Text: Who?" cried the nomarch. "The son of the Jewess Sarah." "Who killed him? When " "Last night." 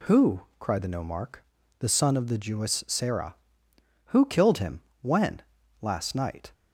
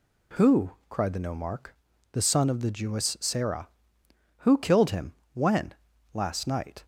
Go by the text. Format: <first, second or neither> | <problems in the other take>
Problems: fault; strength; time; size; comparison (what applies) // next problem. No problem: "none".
neither | none